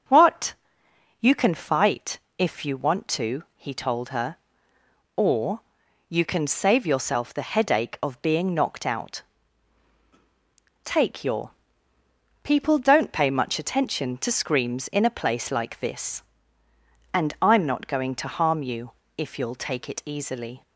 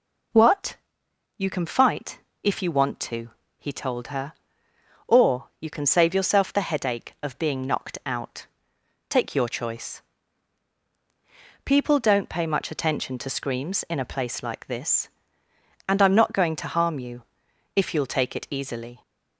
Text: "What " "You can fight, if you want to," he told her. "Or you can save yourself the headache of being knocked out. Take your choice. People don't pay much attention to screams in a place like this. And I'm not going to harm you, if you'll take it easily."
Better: second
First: starts louder than the rest; until 1.4 s; 6.5 dB // pauses between "Or" and "you"; noticeable; at 5.6 s; 0.46 s long // skips "choice"; at 11.9 s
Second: none

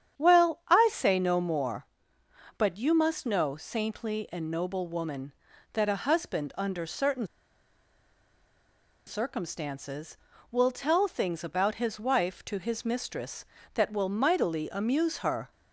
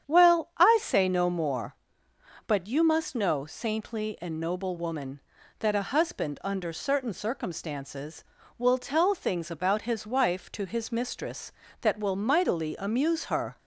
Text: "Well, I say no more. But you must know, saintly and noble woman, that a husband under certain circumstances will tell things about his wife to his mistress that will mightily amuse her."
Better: second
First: starts louder than the rest; strong; until 1.3 s; 9 dB // pauses between "certain" and "circumstances"; strong; at 7.2 s; 1.7 s long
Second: starts louder than the rest; strong; until 1.2 s; 8.5 dB

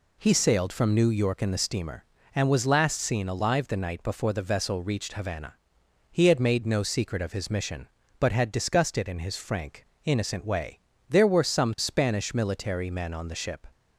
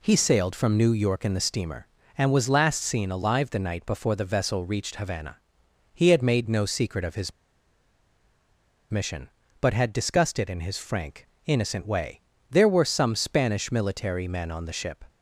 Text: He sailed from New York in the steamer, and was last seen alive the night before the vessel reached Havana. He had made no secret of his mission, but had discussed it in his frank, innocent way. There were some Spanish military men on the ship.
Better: first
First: none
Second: pauses between "his" and "mission"; strong; at 7.3 s; 1.5 s long

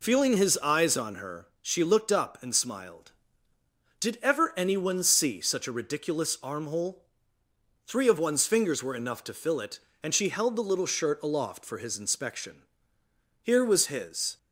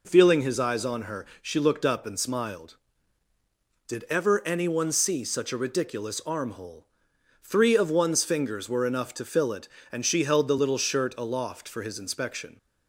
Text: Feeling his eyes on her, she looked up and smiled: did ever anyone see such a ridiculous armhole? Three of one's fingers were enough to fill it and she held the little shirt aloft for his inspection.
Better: second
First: goes on to say "Here was his"; noticeable; from 13.4 s on; 0.94 s long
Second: none

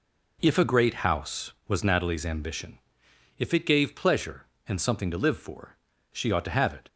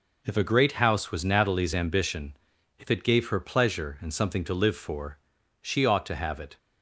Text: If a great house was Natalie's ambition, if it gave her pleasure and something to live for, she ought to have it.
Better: second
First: skips "her"; at 3.9 s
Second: none

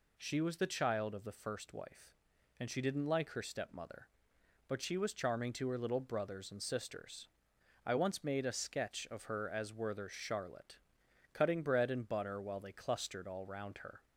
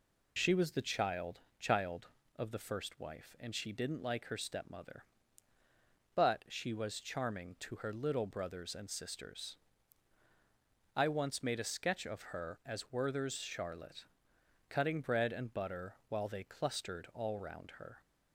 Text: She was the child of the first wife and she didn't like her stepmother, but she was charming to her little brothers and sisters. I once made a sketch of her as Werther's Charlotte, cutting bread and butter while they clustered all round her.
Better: first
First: none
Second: says "child" twice; at 1.5 s

